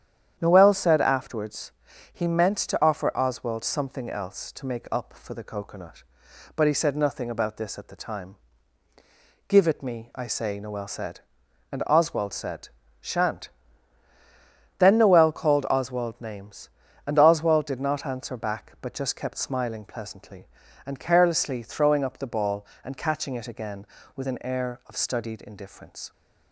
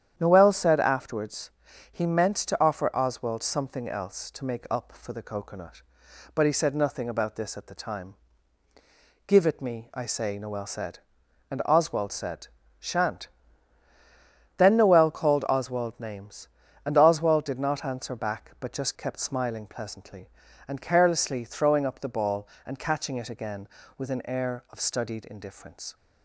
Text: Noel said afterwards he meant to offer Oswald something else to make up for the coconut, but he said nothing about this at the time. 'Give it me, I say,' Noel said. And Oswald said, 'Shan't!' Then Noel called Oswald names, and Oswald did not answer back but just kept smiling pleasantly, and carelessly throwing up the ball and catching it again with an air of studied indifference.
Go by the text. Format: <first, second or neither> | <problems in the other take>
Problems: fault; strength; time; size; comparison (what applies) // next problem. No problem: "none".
neither | starts louder than the rest; strong; the same in both // pauses between "afterwards" and "he"; the same in both